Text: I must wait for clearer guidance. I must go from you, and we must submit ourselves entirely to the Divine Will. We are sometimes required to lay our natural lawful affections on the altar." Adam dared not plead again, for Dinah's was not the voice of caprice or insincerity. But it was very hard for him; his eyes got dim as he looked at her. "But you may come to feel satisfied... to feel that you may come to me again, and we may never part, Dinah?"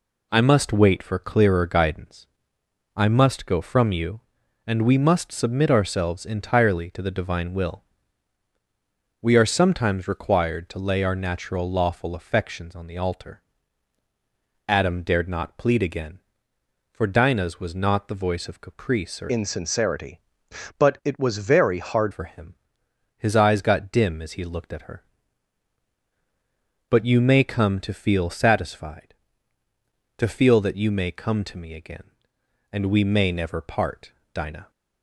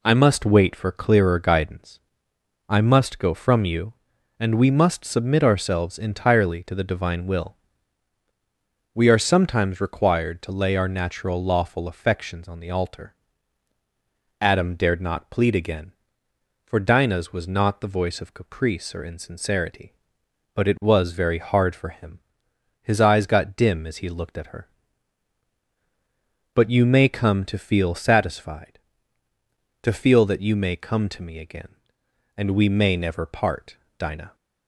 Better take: second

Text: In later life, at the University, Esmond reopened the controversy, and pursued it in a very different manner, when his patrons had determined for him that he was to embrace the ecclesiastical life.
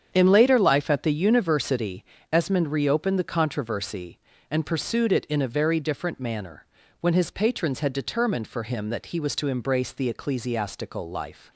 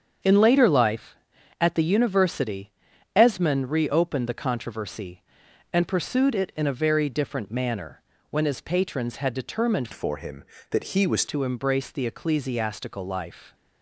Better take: first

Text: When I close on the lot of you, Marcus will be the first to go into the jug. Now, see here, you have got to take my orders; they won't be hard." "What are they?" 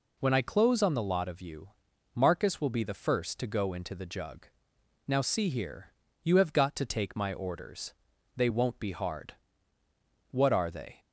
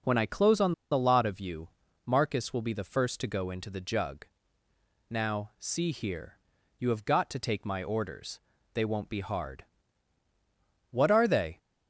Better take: first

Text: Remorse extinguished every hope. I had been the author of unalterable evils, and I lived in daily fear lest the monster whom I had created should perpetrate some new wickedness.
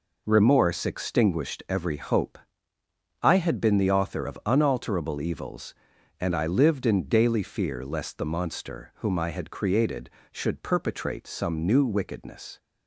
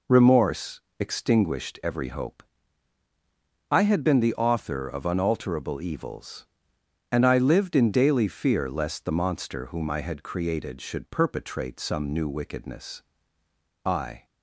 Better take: first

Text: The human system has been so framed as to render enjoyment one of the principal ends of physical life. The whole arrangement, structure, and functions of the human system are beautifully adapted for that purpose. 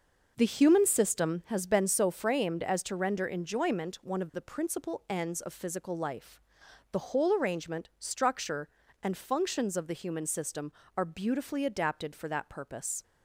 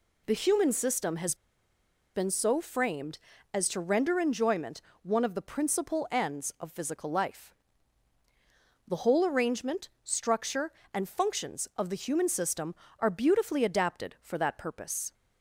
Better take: first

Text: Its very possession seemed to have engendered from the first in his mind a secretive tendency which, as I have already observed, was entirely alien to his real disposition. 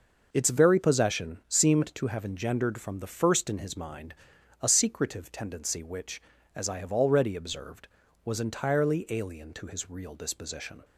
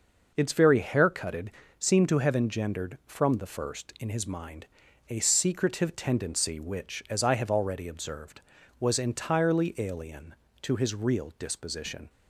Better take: first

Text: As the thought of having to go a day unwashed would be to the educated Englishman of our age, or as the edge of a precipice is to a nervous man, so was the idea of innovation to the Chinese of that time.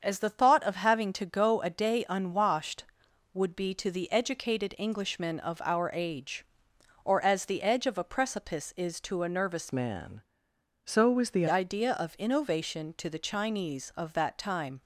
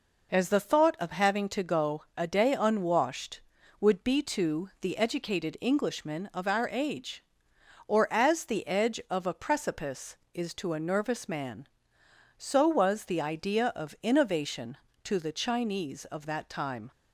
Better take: second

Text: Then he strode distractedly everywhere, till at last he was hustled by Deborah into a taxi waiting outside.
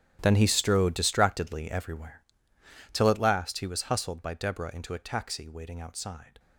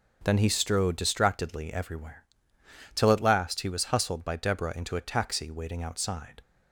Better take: second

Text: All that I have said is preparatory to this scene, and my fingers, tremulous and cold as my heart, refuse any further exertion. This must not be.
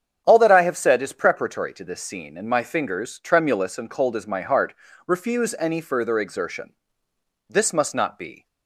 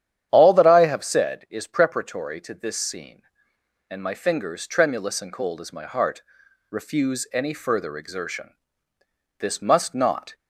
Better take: first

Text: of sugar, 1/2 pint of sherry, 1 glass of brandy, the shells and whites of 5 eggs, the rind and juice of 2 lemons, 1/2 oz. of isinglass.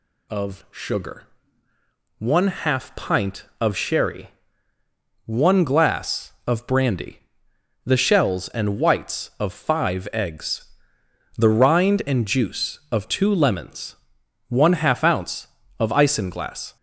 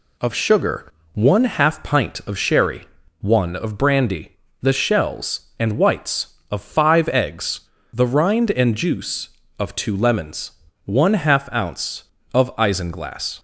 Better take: first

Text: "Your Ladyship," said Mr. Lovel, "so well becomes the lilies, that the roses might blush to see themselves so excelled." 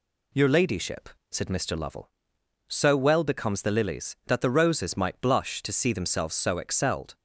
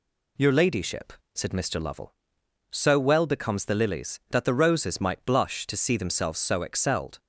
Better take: neither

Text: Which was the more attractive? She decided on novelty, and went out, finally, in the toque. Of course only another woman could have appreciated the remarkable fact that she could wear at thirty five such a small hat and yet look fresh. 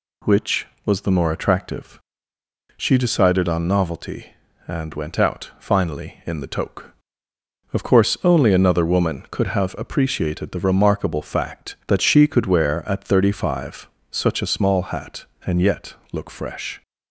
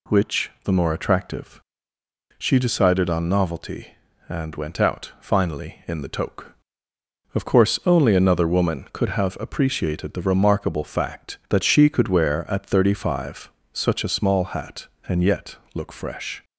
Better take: first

